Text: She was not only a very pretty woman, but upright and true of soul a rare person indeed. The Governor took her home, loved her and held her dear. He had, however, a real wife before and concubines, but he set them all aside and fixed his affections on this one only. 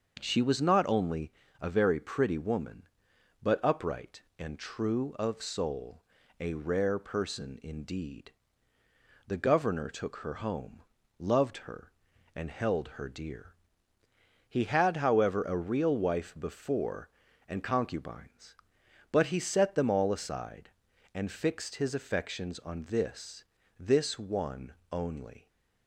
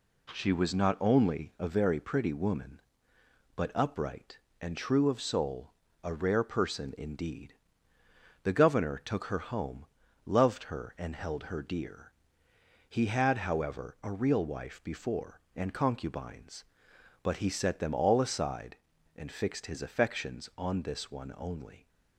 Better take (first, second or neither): second